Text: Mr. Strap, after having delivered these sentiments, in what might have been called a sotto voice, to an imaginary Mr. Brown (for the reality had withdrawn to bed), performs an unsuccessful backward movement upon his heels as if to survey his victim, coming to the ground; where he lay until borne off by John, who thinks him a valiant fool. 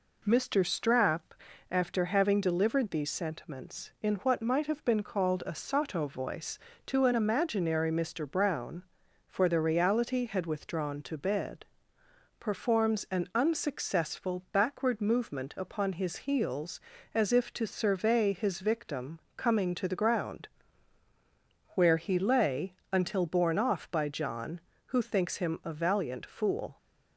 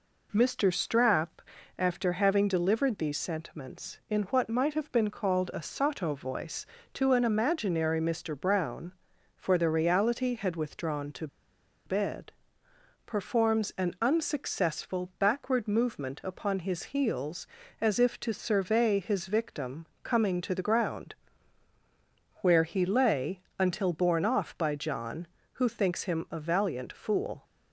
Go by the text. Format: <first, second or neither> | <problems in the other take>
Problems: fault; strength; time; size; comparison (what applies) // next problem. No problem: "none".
first | pauses between "to" and "bed"; noticeable; at 11.2 s; 0.59 s long // pauses between "lay" and "until"; slight; at 23.4 s; 0.18 s long; slight in the first